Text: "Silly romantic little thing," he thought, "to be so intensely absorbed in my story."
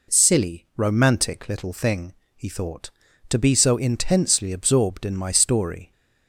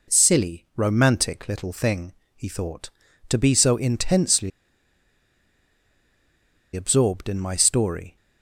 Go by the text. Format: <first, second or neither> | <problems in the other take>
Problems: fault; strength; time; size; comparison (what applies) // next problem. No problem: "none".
first | pauses between "intensely" and "absorbed"; strong; at 4.5 s; 2.2 s long